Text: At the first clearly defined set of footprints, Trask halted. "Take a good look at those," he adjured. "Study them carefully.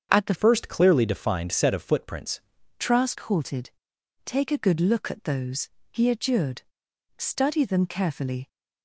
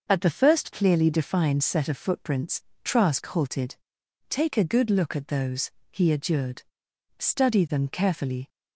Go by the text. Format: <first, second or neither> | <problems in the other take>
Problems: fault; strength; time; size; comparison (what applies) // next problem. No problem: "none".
second | starts louder than the rest; strong; until 1.1 s; 7.5 dB; noticeable in the second // changes voice from "first" to "footprints"; from 0.3 to 2.4 s; 2.1 s long